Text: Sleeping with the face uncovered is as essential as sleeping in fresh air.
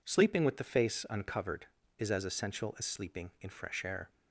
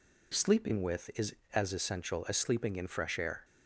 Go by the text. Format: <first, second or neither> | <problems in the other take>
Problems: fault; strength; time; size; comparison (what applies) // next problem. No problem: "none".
first | skips "the face uncovered"; at 1.1 s